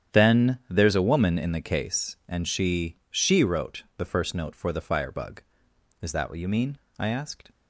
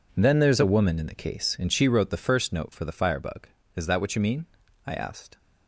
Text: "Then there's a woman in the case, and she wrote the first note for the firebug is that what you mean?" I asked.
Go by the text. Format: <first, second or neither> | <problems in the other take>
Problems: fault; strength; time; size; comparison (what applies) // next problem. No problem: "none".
second | starts louder than the rest; strong; until 1.2 s; 9 dB // says "she" twice; at 3.1 s